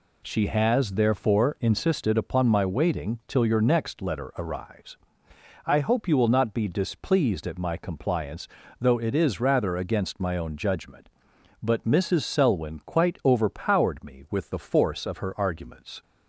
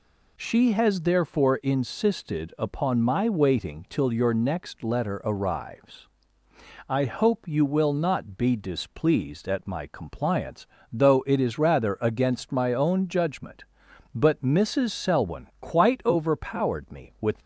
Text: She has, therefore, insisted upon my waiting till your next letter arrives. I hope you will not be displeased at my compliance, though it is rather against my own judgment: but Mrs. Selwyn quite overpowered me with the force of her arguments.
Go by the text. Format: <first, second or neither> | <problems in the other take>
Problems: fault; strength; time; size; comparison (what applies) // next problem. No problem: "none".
first | stops before "the force of her arguments"; at 17.3 s